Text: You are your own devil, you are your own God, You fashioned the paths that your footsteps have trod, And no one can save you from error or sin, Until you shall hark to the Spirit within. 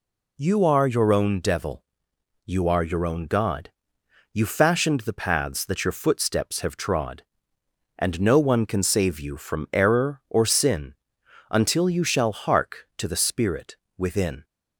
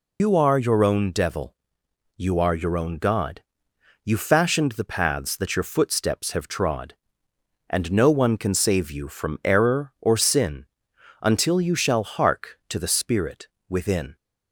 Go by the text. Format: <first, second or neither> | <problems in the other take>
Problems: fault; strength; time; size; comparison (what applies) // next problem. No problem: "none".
first | loses the start of "You"; at 0.1 s; 105 ms // pauses between "Spirit" and "within"; slight; at 13.4 s; 0.20 s long; slight in the first